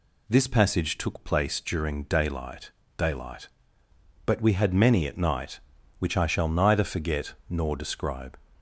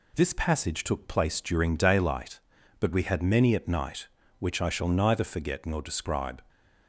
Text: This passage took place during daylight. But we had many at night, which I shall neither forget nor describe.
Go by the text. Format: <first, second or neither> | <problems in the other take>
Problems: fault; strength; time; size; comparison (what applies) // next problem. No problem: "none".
second | says "daylight" twice; at 2.9 s // pauses between "forget" and "nor"; slight; at 7.3 s; 0.16 s long